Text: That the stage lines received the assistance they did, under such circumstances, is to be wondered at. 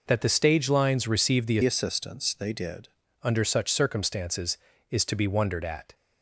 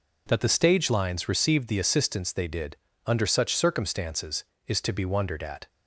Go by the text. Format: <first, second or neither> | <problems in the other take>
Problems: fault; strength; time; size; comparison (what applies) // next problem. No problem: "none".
second | changes voice from "assistance" to "did"; from 1.6 to 2.8 s; 1.2 s long